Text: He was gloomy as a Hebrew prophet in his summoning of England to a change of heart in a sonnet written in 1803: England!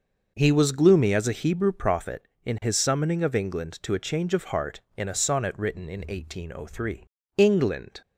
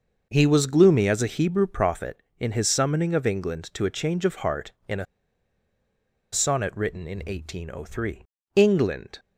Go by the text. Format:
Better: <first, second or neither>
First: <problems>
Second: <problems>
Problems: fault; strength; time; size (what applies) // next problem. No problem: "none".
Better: first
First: none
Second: pauses between "a" and "sonnet"; strong; at 5.0 s; 1.2 s long